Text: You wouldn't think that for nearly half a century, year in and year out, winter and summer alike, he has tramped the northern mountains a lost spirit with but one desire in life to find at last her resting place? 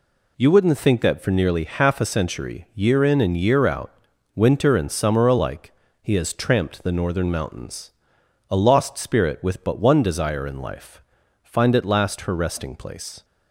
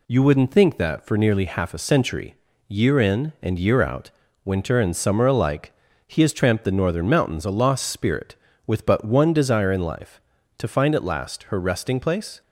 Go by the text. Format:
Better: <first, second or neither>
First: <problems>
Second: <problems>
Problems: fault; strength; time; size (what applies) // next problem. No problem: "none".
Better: second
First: pauses between "mountains" and "a"; noticeable; at 7.9 s; 0.60 s long // skips "to"; at 11.2 s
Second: none